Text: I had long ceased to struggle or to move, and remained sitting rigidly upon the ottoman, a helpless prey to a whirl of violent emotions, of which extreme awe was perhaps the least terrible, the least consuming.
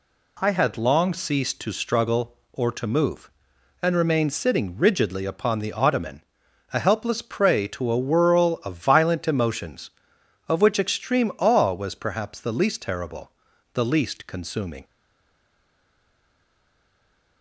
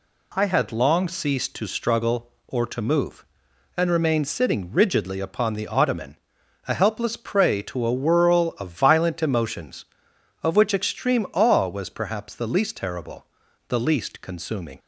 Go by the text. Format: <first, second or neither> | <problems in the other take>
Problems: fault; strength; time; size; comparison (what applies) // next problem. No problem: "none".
second | stays silent after the last word; strong; from 14.8 s on; 2.6 s long